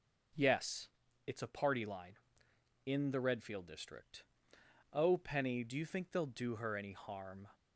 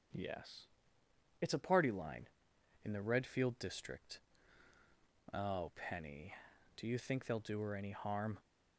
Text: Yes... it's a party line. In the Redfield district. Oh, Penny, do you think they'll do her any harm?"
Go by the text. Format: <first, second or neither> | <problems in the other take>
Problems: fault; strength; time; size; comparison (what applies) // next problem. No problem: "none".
neither | starts louder than the rest; the same in both